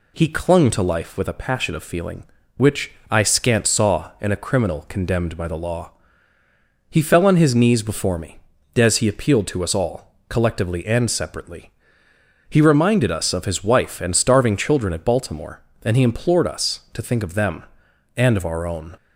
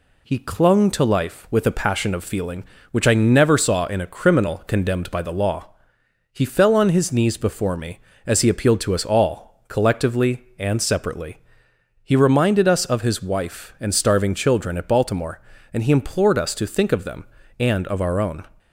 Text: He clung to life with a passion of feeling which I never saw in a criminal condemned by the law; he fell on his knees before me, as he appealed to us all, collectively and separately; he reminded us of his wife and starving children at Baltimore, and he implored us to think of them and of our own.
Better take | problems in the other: second | pauses between "which" and "I"; slight; at 2.9 s; 0.18 s long // says "scant" for "never"; at 3.2 s

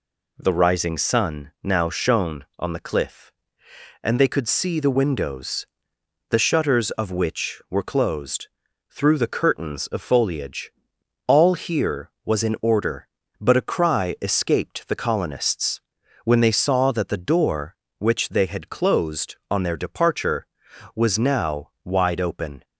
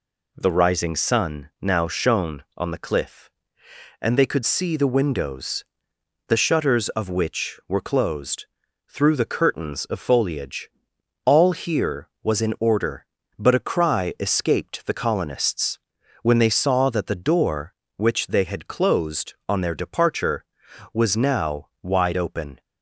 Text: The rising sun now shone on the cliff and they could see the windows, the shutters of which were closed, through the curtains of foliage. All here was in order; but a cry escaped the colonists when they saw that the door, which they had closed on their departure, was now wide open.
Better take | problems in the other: neither | pauses between "colonists" and "when"; the same in both

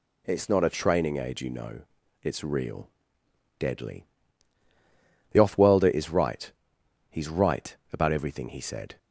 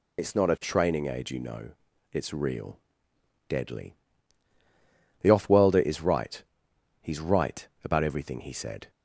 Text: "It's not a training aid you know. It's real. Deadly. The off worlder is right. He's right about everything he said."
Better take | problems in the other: first | loses the start of "It's"; at 0.1 s; 60 ms // pauses between "right" and "about"; slight; at 7.6 s; 0.16 s long; slight in the first

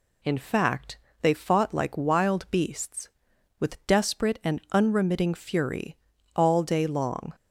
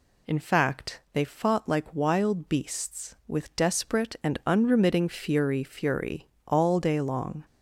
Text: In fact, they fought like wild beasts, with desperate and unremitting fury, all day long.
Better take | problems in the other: first | says "fury" twice; at 5.6 s

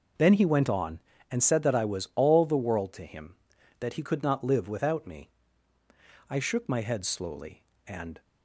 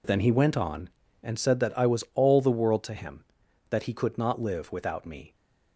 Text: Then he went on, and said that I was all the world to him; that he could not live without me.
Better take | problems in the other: second | goes on to say "I shook my head slowly and"; strong; from 6.2 s on; 1.9 s long

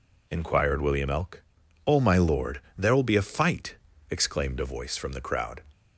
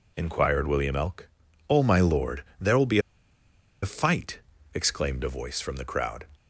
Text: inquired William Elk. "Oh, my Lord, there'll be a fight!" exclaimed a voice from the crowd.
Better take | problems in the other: first | pauses between "be" and "a"; noticeable; at 2.9 s; 0.83 s long

